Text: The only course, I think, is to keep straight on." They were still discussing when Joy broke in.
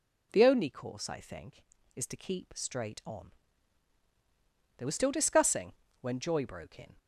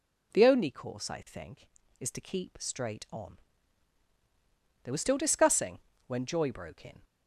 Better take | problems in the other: neither | pauses between "discussing" and "when"; slight; the same in both

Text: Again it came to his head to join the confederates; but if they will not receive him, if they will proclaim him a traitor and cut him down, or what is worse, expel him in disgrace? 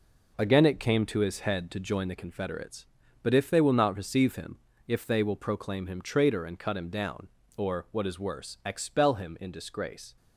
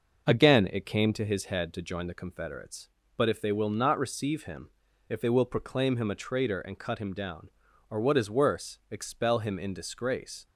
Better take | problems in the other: second | skips "a"; at 6.0 s

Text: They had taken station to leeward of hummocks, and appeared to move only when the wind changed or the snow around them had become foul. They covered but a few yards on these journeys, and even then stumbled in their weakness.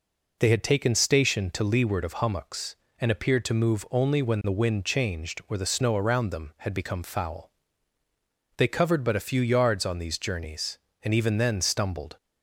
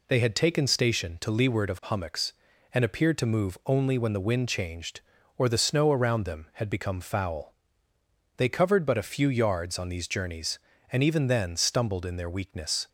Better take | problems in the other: second | stops before "in their weakness"; at 12.1 s

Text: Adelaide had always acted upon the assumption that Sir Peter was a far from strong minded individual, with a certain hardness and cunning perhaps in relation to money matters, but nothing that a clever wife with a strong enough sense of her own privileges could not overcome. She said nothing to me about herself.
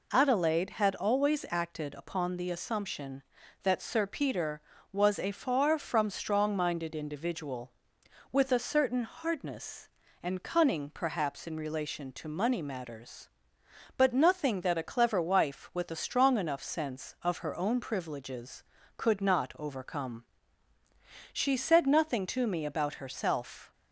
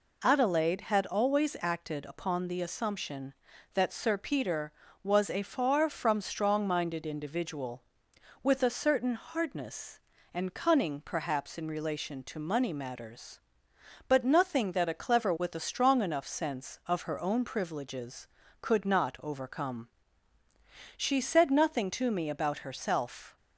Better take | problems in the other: first | skips "wife"; at 15.3 s

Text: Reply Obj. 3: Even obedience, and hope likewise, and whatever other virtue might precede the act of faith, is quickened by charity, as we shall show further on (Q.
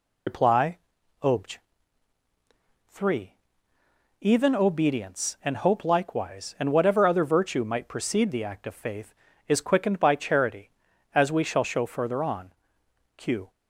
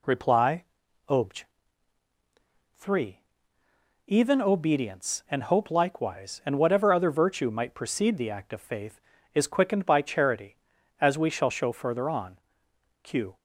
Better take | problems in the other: second | loses the start of "Reply"; at 0.2 s; 85 ms // pauses between "Reply" and "Obj"; at 0.7 s; 0.44 s long; also in the second

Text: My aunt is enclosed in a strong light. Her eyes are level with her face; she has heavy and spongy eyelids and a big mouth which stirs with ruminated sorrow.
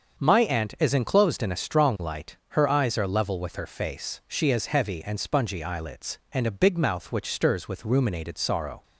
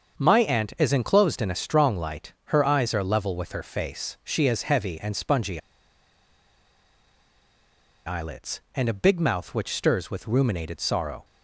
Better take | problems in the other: first | starts louder than the rest; until 1.2 s; 7 dB; also in the first // pauses between "spongy" and "eyelids"; strong; at 5.6 s; 2.4 s long

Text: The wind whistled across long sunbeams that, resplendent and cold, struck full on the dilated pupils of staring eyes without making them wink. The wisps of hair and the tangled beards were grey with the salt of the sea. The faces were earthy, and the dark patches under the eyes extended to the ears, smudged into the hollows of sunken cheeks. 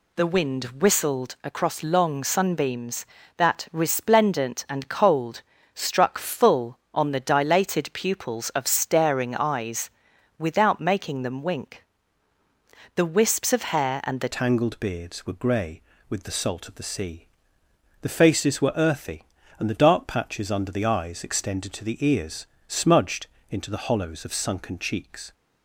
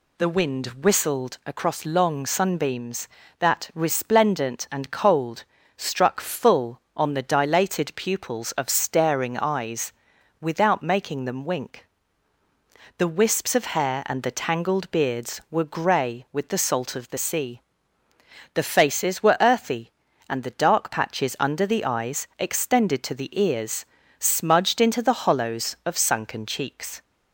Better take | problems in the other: second | pauses between "eyes" and "without"; noticeable; at 9.8 s; 0.48 s long; noticeable in the second // changes voice at "tangled"; from 14.3 s on; 11.0 s long // pauses between "smudged" and "into"; slight; at 23.2 s; 0.24 s long

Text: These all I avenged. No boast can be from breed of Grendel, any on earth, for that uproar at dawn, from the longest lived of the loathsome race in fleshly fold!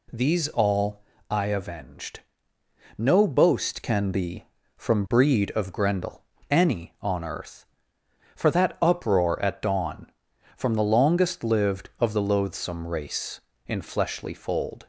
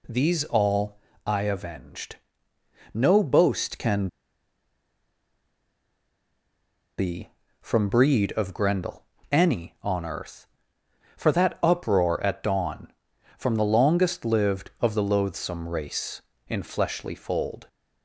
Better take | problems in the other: first | pauses between "all" and "I"; slight; at 0.9 s; 0.26 s long; slight in the first // pauses between "can" and "be"; strong; at 4.0 s; 2.9 s long

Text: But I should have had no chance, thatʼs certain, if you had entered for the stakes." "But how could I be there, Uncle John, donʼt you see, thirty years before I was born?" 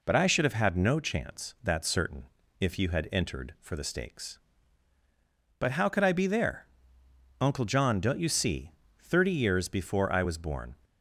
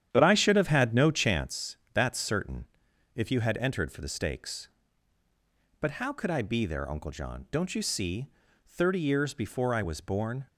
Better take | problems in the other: first | starts louder than the rest; strong; until 1.5 s; 10 dB

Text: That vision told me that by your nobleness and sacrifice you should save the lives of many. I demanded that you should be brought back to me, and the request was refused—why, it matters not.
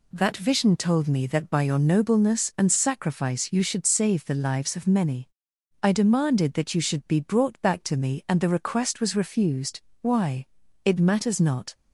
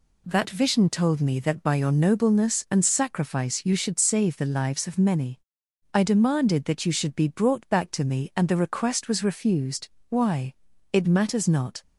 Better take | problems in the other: neither | none

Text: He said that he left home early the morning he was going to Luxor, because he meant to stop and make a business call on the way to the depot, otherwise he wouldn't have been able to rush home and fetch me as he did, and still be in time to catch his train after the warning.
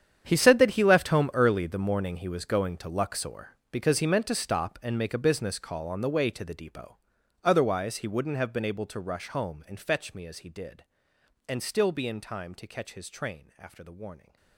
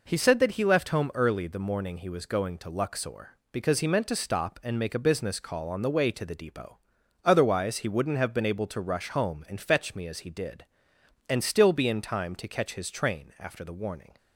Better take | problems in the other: second | gets quieter; strong; throughout; 16.5 dB

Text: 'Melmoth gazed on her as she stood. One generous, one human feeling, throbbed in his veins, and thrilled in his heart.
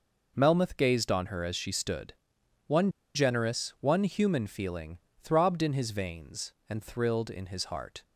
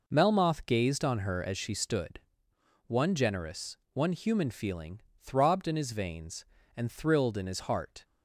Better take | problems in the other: second | pauses between "One" and "generous"; slight; at 2.8 s; 0.25 s long

